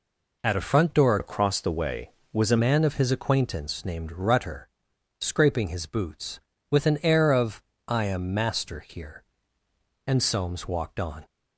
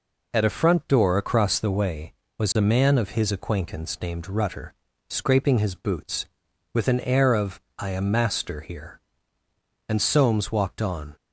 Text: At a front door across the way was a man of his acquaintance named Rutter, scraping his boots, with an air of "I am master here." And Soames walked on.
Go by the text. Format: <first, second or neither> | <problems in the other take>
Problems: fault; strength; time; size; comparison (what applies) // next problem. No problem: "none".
second | changes voice from "across" to "a"; from 1.1 to 2.5 s; 1.4 s long // pauses between "of" and "I"; slight; at 7.6 s; 0.26 s long; slight in the second